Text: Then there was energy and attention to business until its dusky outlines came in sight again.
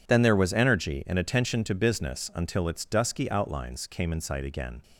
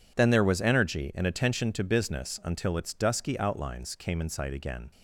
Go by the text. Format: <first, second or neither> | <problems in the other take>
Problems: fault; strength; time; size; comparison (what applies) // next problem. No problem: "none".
neither | none